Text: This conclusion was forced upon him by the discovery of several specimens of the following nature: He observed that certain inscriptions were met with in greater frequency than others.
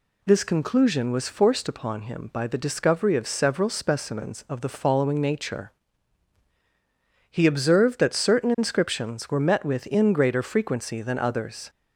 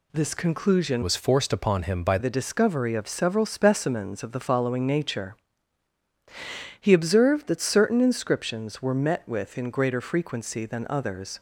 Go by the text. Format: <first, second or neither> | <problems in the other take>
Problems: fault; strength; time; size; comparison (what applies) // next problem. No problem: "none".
first | changes voice from "was" to "by"; from 1.0 to 2.1 s; 1.1 s long